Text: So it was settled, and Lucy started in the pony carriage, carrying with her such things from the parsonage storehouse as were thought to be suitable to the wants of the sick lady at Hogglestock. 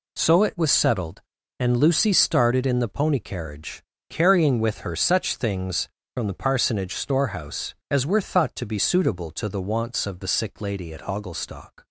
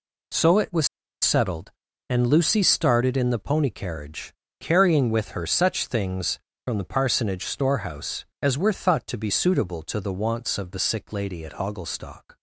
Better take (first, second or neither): first